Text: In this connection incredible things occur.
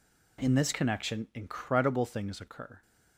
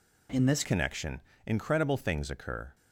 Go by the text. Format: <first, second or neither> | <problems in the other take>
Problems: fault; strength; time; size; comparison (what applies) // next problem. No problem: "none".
first | changes voice at "connection"; from 0.6 s on; 2.1 s long // pauses between "connection" and "incredible"; slight; at 1.2 s; 0.26 s long